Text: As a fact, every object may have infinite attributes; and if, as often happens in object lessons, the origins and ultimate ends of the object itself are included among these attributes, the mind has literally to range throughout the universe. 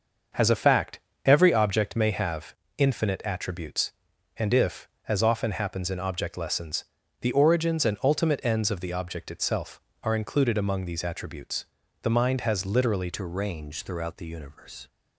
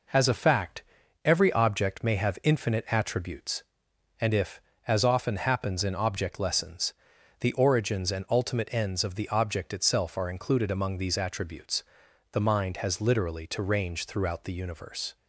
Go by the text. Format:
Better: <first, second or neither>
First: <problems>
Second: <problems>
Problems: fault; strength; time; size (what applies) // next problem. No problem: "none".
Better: second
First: starts louder than the rest; until 1.6 s; 6.5 dB // pauses between "have" and "infinite"; slight; at 2.5 s; 0.22 s long // changes voice at "to"; from 13.1 s on; 1.7 s long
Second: none